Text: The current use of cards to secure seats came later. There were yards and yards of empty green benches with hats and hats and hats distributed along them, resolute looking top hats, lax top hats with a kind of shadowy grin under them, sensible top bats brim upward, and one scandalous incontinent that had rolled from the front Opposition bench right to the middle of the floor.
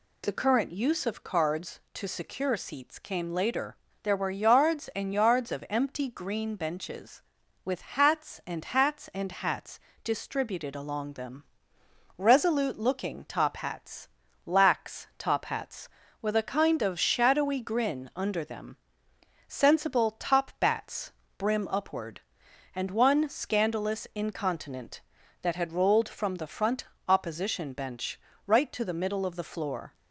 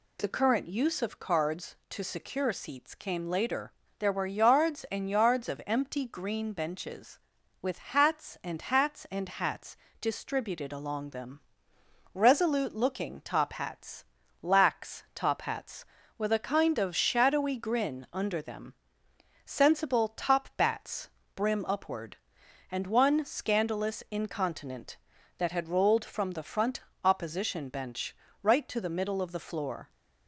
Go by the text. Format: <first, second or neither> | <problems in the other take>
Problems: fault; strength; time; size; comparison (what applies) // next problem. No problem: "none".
neither | pauses between "hats" and "distributed"; slight; the same in both // pauses between "bats" and "brim"; slight; the same in both // pauses between "front" and "Opposition"; slight; the same in both // pauses between "bench" and "right"; slight; the same in both